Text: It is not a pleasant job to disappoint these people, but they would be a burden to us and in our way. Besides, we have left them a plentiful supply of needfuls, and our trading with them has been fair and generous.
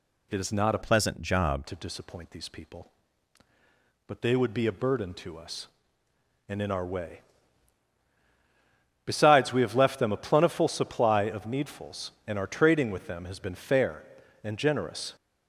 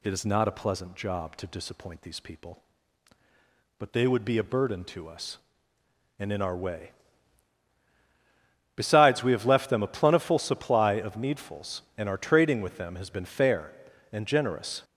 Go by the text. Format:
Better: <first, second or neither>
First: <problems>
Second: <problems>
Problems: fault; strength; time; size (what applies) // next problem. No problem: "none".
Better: second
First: changes voice from "pleasant" to "job"; from 0.8 to 1.6 s; 0.8 s long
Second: none